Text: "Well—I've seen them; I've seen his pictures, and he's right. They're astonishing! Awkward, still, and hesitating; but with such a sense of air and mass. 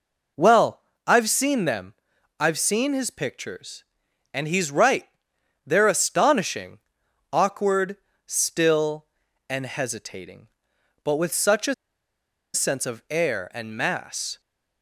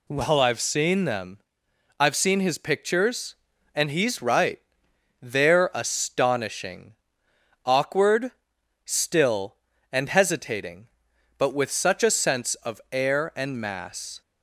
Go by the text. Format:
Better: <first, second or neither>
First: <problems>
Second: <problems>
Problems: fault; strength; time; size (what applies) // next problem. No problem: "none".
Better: second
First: pauses between "a" and "sense"; noticeable; at 11.7 s; 0.79 s long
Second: none